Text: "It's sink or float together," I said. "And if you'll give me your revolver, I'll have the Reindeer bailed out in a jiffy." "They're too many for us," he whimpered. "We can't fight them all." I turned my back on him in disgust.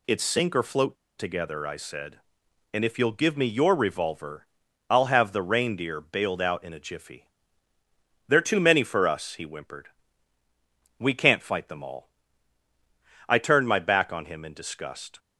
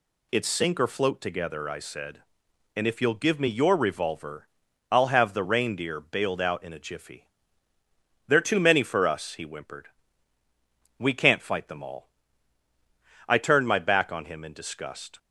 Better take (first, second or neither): second